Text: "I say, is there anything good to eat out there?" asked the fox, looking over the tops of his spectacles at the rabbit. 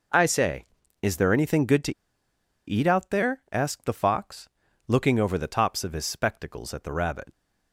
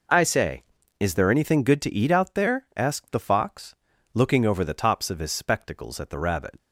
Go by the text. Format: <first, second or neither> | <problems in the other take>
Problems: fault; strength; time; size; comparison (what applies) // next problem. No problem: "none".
second | pauses between "to" and "eat"; noticeable; at 1.9 s; 0.75 s long